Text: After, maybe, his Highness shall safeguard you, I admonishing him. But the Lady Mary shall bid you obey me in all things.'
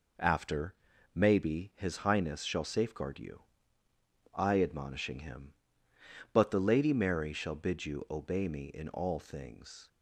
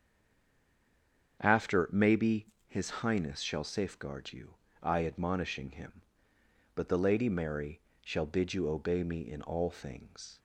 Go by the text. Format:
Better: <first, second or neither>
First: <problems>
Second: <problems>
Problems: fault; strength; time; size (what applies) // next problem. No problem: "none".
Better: first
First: none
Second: stays silent before the first word; noticeable; until 1.3 s; 1.3 s long // starts louder than the rest; strong; until 2.4 s; 7.5 dB // pauses between "Mary" and "shall"; slight; at 7.8 s; 0.24 s long